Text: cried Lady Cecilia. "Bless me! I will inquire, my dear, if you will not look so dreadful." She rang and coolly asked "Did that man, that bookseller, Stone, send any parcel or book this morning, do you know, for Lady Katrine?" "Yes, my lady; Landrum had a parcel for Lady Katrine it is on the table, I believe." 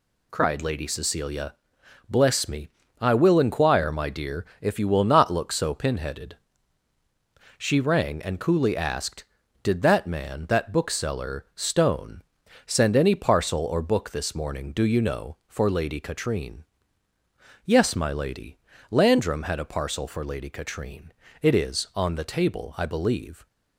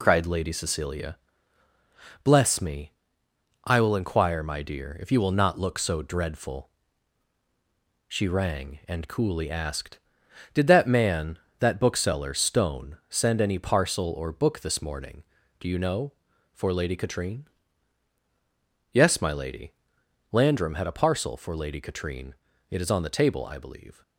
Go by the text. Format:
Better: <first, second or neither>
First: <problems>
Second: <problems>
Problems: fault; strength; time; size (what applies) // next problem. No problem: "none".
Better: second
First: says "pinheaded" for "dreadful"; at 5.7 s // pauses between "Katrine" and "it"; slight; at 21.1 s; 0.30 s long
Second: pauses between "Katrine" and "it"; slight; at 22.3 s; 0.34 s long